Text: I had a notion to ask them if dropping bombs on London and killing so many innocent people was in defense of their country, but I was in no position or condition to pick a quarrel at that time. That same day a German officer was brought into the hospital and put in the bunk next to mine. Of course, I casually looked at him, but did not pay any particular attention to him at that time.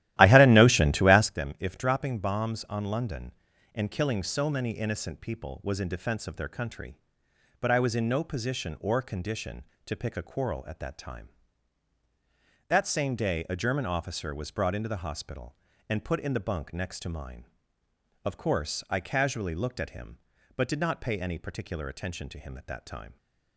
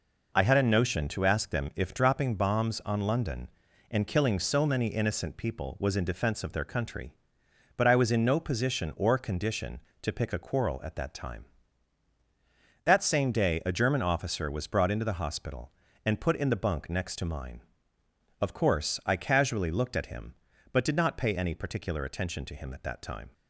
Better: second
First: starts louder than the rest; strong; until 1.4 s; 14.5 dB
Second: none

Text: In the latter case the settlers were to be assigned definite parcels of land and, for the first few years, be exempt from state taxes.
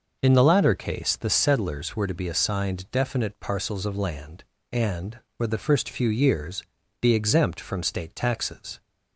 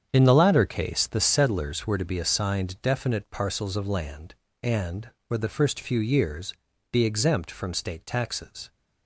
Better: first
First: none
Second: gets quieter; strong; throughout; 10 dB

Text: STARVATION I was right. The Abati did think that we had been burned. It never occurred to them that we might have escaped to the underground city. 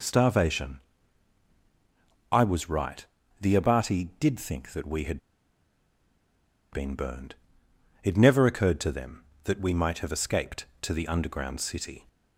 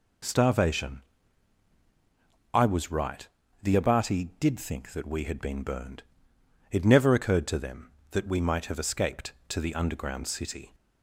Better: second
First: pauses between "STARVATION" and "I"; strong; at 0.7 s; 1.5 s long // pauses between "had" and "been"; strong; at 5.2 s; 1.5 s long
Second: pauses between "STARVATION" and "I"; strong; at 1.0 s; 1.5 s long

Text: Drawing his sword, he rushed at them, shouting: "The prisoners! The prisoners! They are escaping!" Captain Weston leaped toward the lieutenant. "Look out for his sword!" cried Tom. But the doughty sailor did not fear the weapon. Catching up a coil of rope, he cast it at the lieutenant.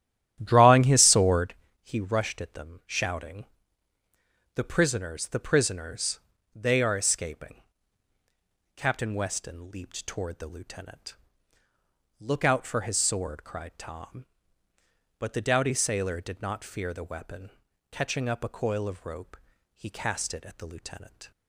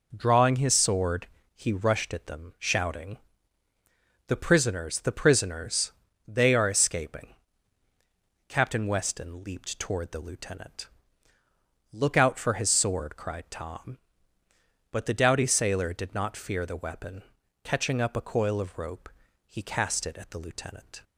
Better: second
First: starts louder than the rest; strong; until 1.5 s; 12 dB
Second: none

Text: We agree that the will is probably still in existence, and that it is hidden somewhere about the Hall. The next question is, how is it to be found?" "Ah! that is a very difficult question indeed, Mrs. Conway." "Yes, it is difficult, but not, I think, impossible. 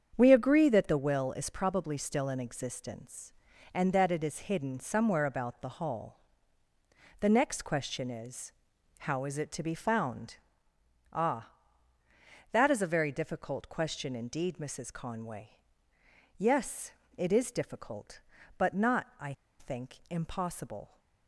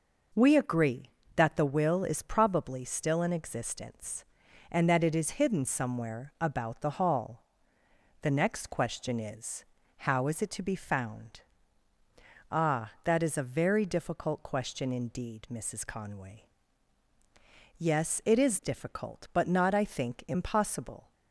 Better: second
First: starts louder than the rest; strong; until 1.1 s; 7.5 dB // pauses between "I" and "think"; slight; at 19.3 s; 0.27 s long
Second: none

